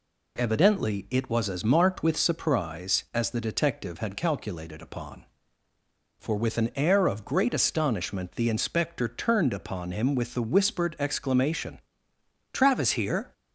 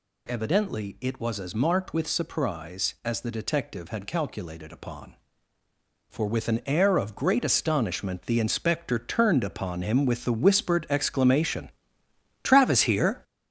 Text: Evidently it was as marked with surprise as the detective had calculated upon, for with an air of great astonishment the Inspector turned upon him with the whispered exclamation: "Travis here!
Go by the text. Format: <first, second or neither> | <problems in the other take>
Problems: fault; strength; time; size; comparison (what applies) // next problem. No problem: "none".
first | gets louder; strong; throughout; 7.5 dB